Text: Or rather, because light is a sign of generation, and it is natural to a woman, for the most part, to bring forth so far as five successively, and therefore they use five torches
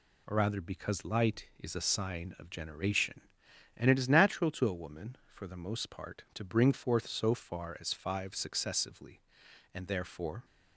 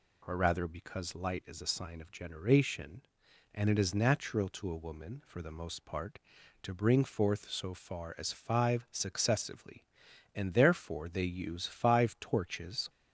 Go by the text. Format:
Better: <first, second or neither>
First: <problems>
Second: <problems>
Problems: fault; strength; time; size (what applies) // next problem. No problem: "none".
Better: second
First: stops before "they use five torches"; at 10.4 s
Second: none